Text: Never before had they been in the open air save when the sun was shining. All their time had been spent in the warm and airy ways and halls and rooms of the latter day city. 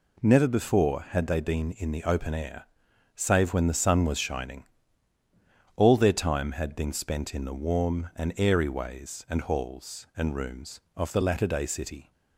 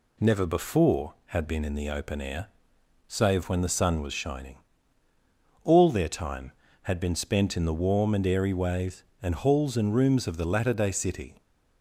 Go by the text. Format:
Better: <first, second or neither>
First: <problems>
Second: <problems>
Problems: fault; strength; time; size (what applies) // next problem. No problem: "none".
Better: first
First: pauses between "air" and "save"; noticeable; at 2.6 s; 0.50 s long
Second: skips "they"; at 1.4 s // pauses between "air" and "save"; noticeable; at 2.4 s; 0.58 s long